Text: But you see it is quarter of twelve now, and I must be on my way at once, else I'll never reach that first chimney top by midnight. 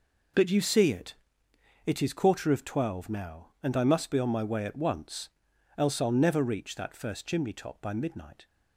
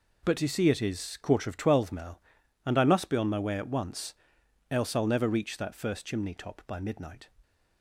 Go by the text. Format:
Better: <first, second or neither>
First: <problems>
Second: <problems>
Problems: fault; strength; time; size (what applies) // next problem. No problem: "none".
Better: second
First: says "it" twice; at 1.8 s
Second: none